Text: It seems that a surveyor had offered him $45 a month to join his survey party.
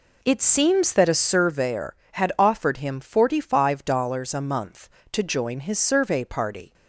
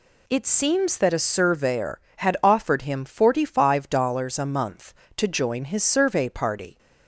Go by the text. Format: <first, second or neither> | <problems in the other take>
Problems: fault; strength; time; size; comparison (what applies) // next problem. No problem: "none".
second | starts louder than the rest; slight; until 1.5 s; 3 dB